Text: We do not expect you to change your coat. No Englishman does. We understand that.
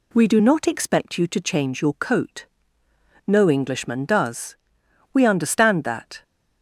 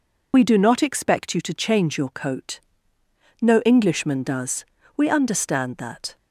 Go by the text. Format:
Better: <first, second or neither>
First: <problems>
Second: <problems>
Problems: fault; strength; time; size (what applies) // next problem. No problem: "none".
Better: first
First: none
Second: loses the start of "We"; at 0.3 s; 50 ms